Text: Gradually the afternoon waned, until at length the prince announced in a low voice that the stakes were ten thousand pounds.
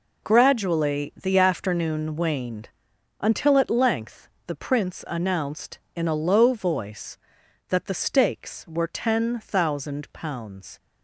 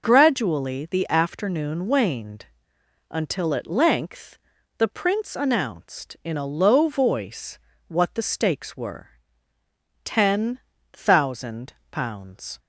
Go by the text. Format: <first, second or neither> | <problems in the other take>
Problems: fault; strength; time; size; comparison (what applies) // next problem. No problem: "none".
first | pauses between "length" and "the"; at 4.3 s; 0.40 s long; slight in the first // says "what" for "that"; at 7.8 s // pauses between "were" and "ten"; noticeable; at 9.0 s; 0.98 s long // pauses between "ten" and "thousand"; slight; at 10.5 s; 0.34 s long // pauses between "thousand" and "pounds"; slight; at 11.7 s; 0.18 s long